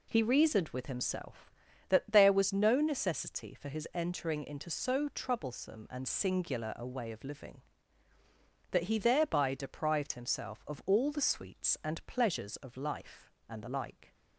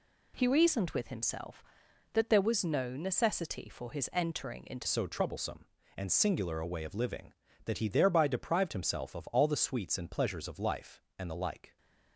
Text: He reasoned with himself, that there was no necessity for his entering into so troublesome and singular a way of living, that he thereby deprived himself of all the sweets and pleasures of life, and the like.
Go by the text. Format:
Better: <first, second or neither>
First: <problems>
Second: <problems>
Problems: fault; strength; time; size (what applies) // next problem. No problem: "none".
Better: first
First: none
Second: changes voice at "so"; from 4.8 s on; 6.9 s long